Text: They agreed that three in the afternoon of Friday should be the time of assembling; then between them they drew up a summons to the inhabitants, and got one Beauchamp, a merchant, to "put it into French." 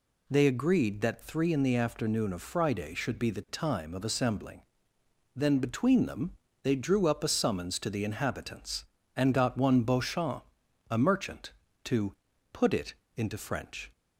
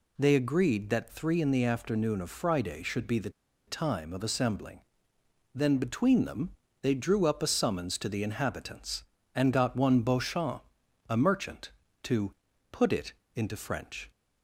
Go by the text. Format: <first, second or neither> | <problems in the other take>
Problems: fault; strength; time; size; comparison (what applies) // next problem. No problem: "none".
first | pauses between "the" and "time"; at 3.2 s; 0.37 s long // pauses between "them" and "they"; slight; at 6.5 s; 0.32 s long; slight in the first // pauses between "to" and "put"; at 12.3 s; 0.40 s long; also in the first // pauses between "it" and "into"; slight; at 13.1 s; 0.24 s long; slight in the first